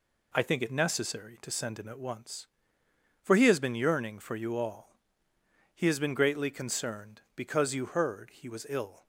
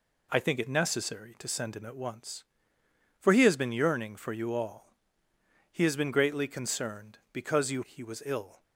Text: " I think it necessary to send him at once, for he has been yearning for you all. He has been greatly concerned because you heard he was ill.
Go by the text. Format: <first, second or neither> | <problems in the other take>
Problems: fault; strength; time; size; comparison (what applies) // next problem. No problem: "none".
first | skips "heard"; at 7.8 s